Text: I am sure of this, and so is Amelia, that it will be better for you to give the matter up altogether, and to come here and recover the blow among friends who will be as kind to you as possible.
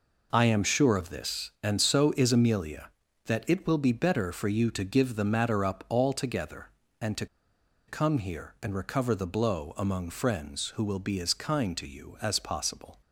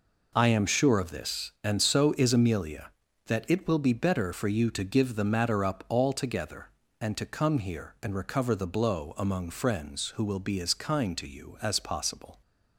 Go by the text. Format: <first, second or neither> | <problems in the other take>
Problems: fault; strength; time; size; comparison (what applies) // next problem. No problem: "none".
second | pauses between "to" and "come"; noticeable; at 7.2 s; 0.62 s long